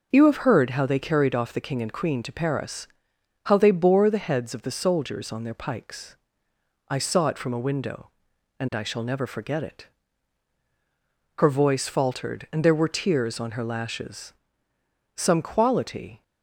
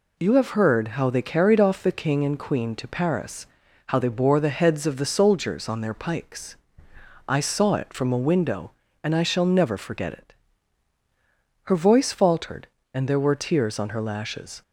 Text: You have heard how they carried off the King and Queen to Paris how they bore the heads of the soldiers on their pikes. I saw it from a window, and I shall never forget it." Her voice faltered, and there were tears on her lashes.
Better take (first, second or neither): second